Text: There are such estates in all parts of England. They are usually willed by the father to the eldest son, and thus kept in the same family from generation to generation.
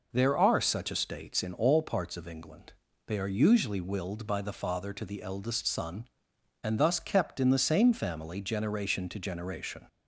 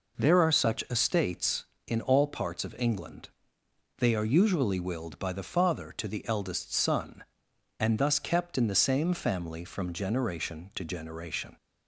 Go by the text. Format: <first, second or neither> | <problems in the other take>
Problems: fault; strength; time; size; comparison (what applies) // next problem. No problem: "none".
second | skips "from"; at 8.4 s